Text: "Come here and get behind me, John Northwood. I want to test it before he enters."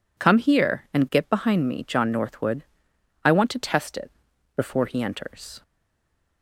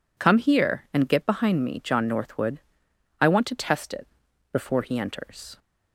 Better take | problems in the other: second | pauses between "it" and "before"; at 4.1 s; 0.44 s long; also in the second // stays silent after the last word; slight; from 5.6 s on; 0.8 s long

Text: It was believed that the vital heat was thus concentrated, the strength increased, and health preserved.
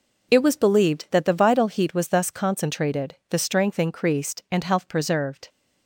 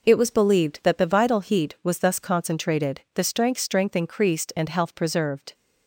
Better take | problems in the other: first | says "strength" twice; at 3.5 s

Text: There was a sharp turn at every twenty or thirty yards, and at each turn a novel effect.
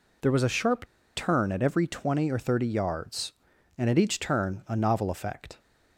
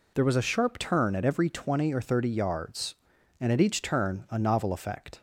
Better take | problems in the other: second | pauses between "sharp" and "turn"; slight; at 0.8 s; 0.29 s long

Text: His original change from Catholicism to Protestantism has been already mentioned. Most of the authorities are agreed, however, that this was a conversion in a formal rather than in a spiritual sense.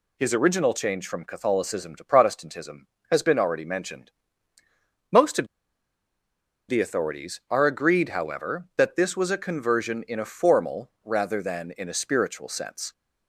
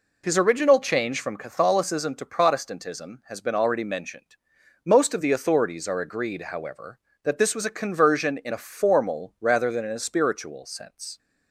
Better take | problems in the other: second | pauses between "of" and "the"; at 5.4 s; 1.2 s long

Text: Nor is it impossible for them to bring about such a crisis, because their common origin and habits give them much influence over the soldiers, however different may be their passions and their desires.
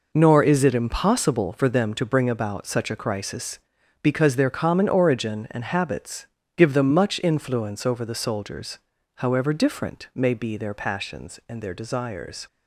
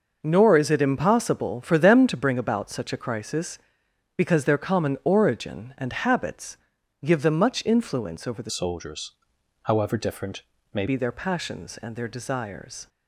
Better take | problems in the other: first | pauses between "habits" and "give"; noticeable; at 6.5 s; 0.48 s long; slight in the first // changes voice from "soldiers" to "may"; from 8.5 to 10.8 s; 2.3 s long // pauses between "different" and "may"; slight; at 10.4 s; 0.30 s long

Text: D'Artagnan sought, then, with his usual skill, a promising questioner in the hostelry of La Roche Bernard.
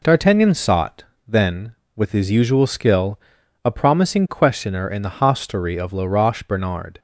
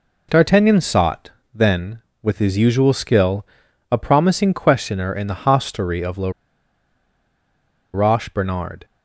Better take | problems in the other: first | pauses between "La" and "Roche"; strong; at 6.2 s; 1.6 s long

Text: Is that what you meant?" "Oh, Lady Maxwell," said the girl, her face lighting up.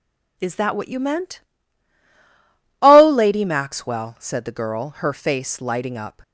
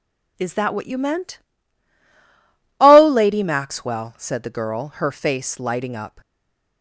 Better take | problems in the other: first | stays silent after the last word; slight; from 6.2 s on; 0.6 s long

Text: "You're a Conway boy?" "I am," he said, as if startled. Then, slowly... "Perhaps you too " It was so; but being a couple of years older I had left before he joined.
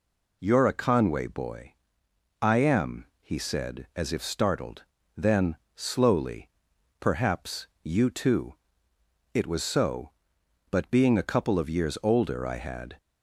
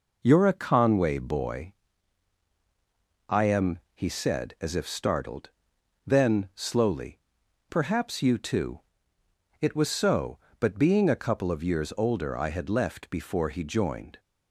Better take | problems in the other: second | pauses between "Perhaps" and "you"; slight; at 7.6 s; 0.16 s long // stops before "left before he joined"; at 12.9 s

